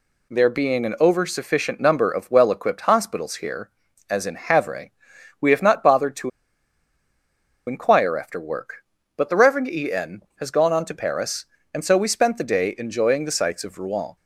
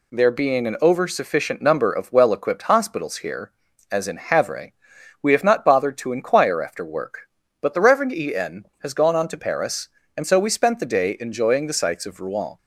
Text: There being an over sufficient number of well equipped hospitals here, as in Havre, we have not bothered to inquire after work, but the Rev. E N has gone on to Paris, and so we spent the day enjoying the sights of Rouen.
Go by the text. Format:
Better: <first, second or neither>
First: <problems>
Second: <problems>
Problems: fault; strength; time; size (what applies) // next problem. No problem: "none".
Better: second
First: pauses between "to" and "inquire"; strong; at 6.3 s; 1.3 s long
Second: none